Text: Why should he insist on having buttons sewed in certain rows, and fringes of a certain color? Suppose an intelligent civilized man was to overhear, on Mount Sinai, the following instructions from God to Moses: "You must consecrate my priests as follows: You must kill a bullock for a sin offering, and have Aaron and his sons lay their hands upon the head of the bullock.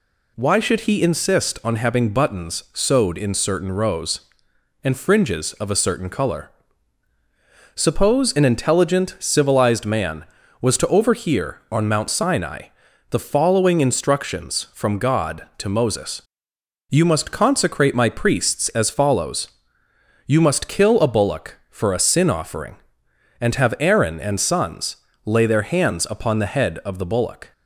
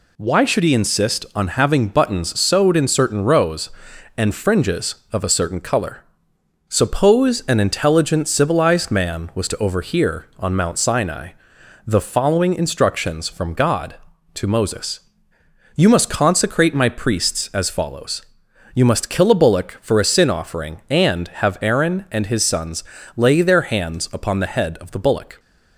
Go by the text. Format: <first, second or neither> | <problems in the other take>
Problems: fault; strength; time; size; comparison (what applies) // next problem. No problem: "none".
second | skips "his"; at 24.3 s // pauses between "sons" and "lay"; slight; at 24.9 s; 0.28 s long; slight in the second